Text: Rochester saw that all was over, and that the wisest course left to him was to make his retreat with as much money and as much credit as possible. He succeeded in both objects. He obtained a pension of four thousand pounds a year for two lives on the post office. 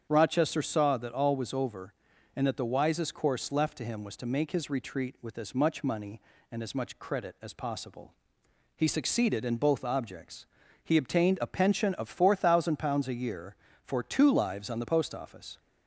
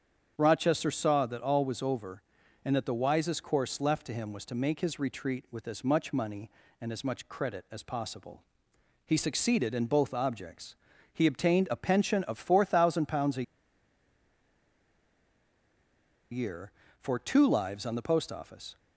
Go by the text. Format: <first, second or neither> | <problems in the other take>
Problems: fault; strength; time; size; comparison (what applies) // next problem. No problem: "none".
first | starts louder than the rest; strong; until 1.3 s; 8 dB; strong in the first // pauses between "a" and "year"; strong; at 13.4 s; 2.8 s long